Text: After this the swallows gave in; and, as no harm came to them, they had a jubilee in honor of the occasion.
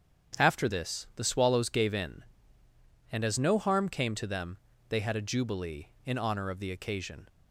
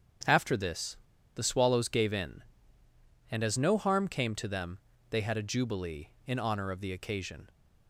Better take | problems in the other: first | starts louder than the rest; strong; until 1.6 s; 8.5 dB; strong in the first // pauses between "this" and "the"; at 0.9 s; 0.39 s long

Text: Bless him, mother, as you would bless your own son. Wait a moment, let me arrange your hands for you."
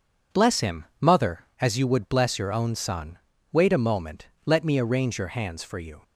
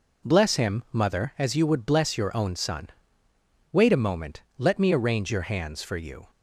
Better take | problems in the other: neither | none

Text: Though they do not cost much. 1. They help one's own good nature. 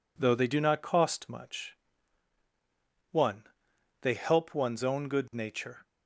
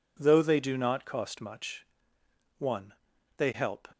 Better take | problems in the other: first | stops before "one's own good nature"; at 3.9 s

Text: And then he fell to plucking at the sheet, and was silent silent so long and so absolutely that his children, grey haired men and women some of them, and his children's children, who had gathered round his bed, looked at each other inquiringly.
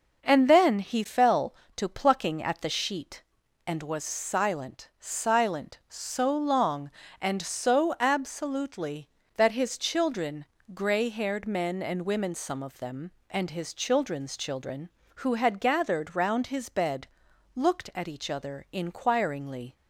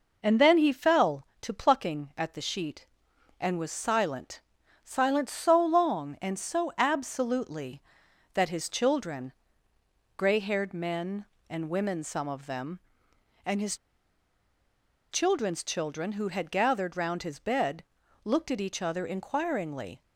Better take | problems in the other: first | pauses between "silent" and "silent"; at 4.4 s; 0.42 s long // pauses between "his" and "children's"; strong; at 13.7 s; 1.3 s long

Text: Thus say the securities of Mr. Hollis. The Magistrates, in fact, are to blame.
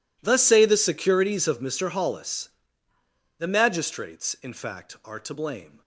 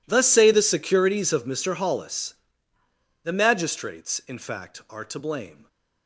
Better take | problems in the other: neither | none

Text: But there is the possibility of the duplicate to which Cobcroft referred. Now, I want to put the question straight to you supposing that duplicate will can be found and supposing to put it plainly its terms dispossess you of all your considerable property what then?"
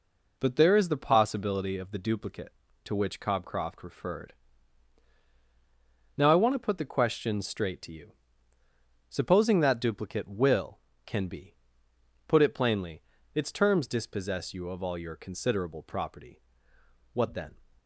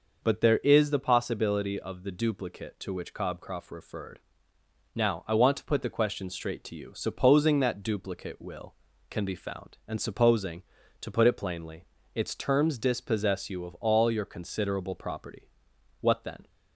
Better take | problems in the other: second | pauses between "you" and "supposing"; noticeable; at 8.1 s; 0.98 s long // skips "found and supposing to"; at 11.9 s // pauses between "plainly" and "its"; slight; at 13.0 s; 0.32 s long; slight in the second // pauses between "property" and "what"; noticeable; at 16.4 s; 0.72 s long; noticeable in the second

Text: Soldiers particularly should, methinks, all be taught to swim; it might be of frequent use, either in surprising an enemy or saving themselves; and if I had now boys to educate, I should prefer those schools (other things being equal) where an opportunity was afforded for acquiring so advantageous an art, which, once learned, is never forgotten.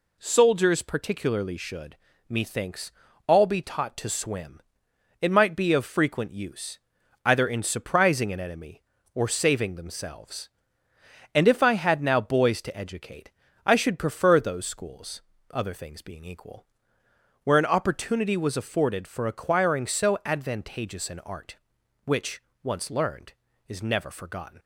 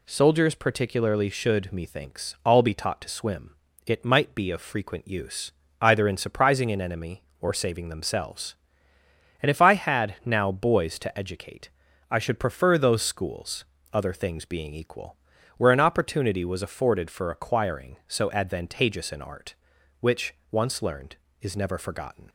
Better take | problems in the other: neither | none

